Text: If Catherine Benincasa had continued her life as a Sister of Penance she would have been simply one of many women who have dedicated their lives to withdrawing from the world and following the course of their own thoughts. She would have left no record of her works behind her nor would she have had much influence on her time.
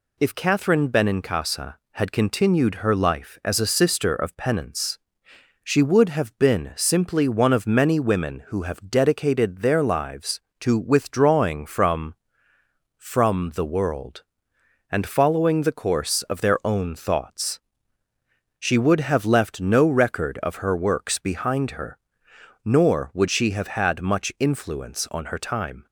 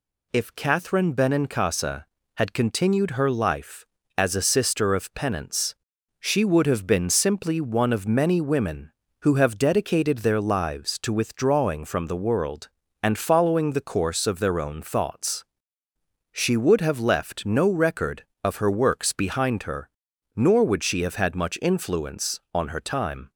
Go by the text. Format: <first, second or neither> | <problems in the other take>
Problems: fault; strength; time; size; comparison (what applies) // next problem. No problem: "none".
second | pauses between "Penance" and "she"; noticeable; at 4.9 s; 0.64 s long; noticeable in the second // says "from" twice; at 12.9 s // pauses between "her" and "nor"; noticeable; at 21.9 s; 0.64 s long; noticeable in the second